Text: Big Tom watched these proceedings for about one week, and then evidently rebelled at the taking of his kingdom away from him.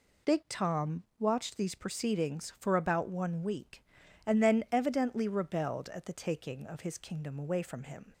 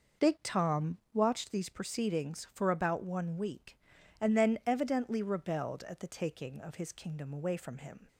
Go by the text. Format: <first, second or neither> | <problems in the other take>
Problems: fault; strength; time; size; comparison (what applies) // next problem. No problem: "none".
first | starts louder than the rest; noticeable; until 1.5 s; 5.5 dB // pauses between "Tom" and "watched"; slight; at 0.9 s; 0.16 s long; slight in the first